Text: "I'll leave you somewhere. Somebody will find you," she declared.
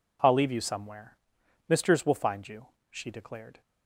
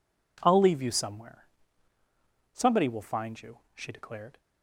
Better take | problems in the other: second | says "Misters" for "Somebody"; at 1.6 s

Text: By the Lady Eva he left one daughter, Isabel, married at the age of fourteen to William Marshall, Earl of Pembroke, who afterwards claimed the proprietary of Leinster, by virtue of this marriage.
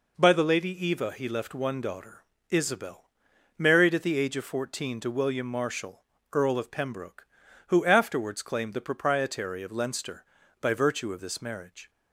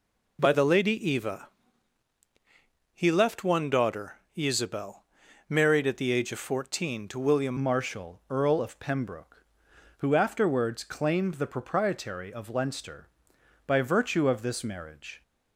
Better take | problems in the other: first | pauses between "Eva" and "he"; strong; at 1.4 s; 1.4 s long // changes voice at "Marshall"; from 7.6 s on; 7.6 s long

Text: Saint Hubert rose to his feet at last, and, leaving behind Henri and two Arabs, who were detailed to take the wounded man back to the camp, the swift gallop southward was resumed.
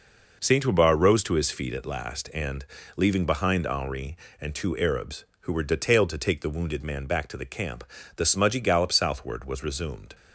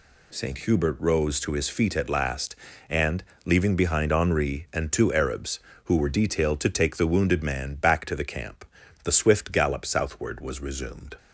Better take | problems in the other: second | says "smudgy" for "swift"; at 8.2 s

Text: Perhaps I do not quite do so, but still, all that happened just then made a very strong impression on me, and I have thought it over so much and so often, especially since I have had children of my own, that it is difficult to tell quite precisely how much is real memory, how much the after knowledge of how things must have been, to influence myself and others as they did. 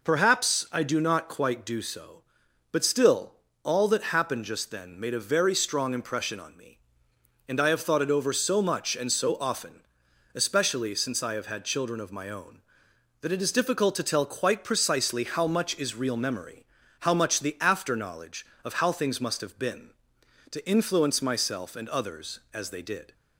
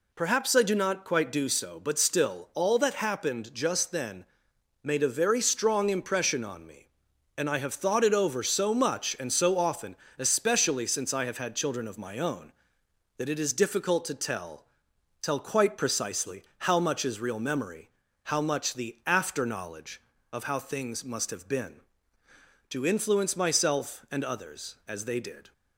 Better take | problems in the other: first | pauses between "then" and "made"; noticeable; at 4.2 s; 0.58 s long // says "tell" twice; at 15.2 s // pauses between "precisely" and "how"; slight; at 16.4 s; 0.16 s long

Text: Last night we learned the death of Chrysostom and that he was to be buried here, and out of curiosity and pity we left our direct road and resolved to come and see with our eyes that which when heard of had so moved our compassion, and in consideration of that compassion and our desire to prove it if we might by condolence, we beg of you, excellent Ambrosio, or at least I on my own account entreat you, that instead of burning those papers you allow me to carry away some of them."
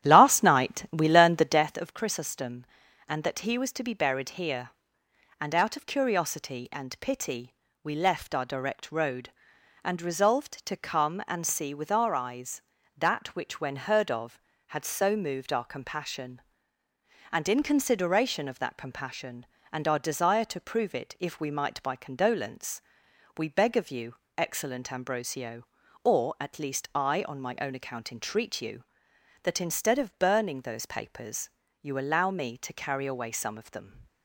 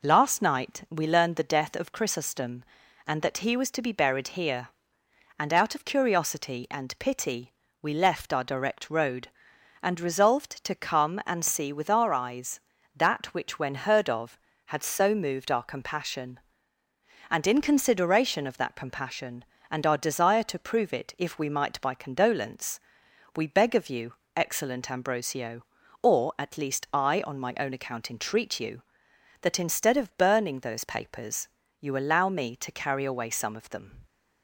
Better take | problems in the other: second | starts louder than the rest; strong; until 1.7 s; 11.5 dB // pauses between "pity" and "we"; slight; at 7.5 s; 0.30 s long; slight in the second // pauses between "papers" and "you"; slight; at 31.4 s; 0.34 s long; slight in the second

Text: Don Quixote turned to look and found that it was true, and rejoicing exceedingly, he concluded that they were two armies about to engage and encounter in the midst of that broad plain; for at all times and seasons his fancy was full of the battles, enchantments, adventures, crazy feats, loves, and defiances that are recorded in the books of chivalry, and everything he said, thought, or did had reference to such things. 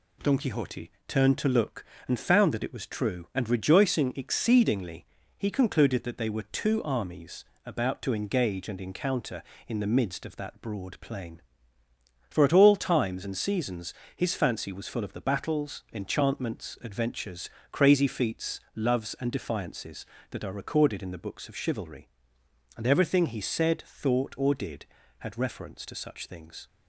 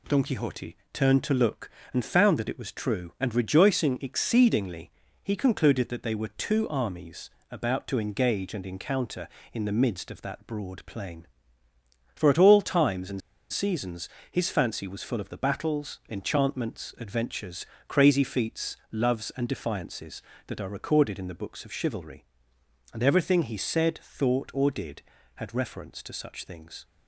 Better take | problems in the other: first | pauses between "Quixote" and "turned"; slight; at 0.7 s; 0.16 s long; slight in the first // pauses between "armies" and "about"; slight; at 7.3 s; 0.20 s long; slight in the first // pauses between "and" and "seasons"; slight; at 13.2 s; 0.32 s long // pauses between "seasons" and "his"; slight; at 14.0 s; 0.20 s long; slight in the first

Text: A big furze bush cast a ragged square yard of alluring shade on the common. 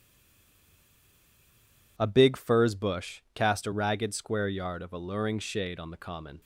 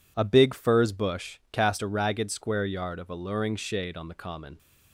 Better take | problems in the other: second | stays silent before the first word; noticeable; until 1.9 s; 1.9 s long

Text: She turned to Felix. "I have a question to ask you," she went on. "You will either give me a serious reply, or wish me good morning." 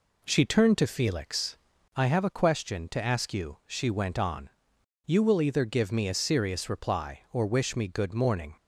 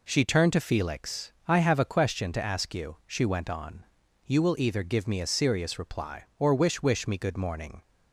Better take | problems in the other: first | says "wish" twice; at 6.8 s

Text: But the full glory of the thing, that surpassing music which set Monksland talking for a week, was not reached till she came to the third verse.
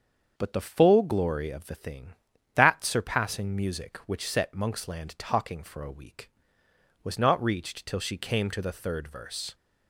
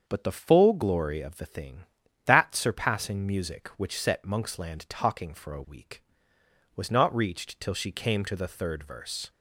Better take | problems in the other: neither | starts louder than the rest; the same in both

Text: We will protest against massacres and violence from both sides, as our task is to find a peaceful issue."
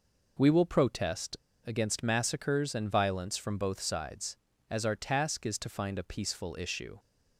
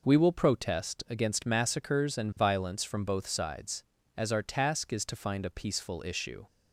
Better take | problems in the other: second | pauses between "protest" and "against"; slight; at 1.3 s; 0.29 s long

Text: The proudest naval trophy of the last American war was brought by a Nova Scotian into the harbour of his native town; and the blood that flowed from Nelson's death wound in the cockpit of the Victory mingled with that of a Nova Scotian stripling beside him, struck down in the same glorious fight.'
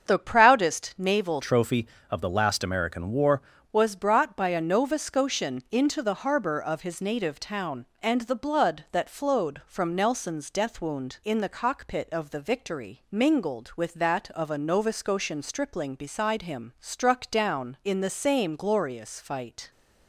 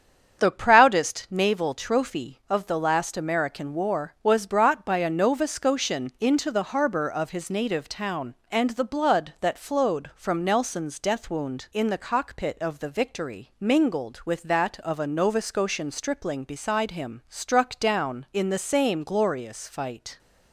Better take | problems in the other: second | starts louder than the rest; strong; until 1.0 s; 7.5 dB; strong in the second // changes voice from "trophy" to "war"; from 1.4 to 3.3 s; 1.9 s long

